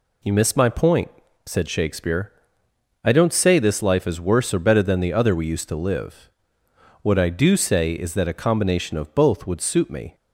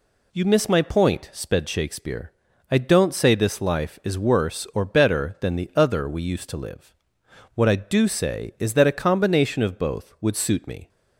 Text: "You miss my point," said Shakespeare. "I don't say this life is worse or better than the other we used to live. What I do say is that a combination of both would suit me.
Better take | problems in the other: first | says "sped" for "said"; at 1.3 s

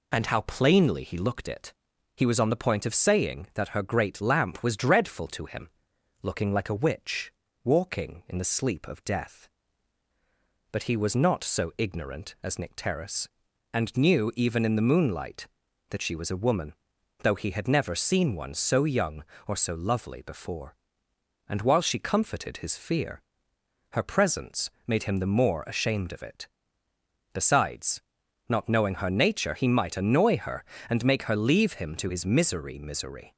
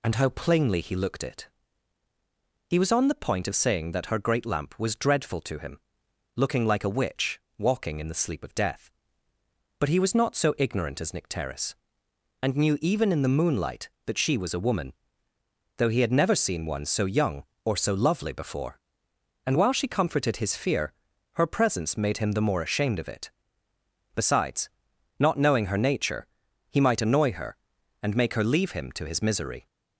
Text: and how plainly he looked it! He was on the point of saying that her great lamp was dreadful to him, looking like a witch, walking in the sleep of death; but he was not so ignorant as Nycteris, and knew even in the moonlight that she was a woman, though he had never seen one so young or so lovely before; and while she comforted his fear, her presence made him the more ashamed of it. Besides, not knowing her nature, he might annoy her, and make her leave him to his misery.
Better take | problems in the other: second | pauses between "presence" and "made"; slight; at 24.6 s; 0.16 s long // says "misery" twice; at 32.7 s

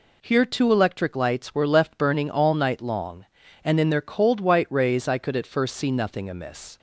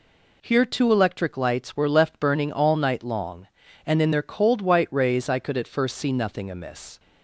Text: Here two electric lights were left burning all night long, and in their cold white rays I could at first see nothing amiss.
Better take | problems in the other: neither | none

